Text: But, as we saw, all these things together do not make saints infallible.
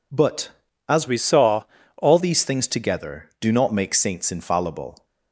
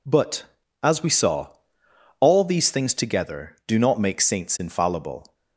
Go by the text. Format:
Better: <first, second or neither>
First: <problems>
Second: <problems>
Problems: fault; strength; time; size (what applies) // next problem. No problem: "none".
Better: second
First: changes voice from "we" to "all"; from 1.0 to 2.1 s; 1.1 s long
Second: none